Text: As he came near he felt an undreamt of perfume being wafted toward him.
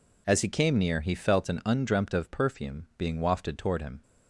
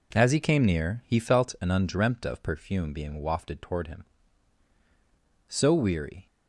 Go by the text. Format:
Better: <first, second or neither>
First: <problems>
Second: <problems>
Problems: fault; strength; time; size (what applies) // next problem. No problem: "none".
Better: first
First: none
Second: goes on to say "So weary"; noticeable; from 5.4 s on; 0.78 s long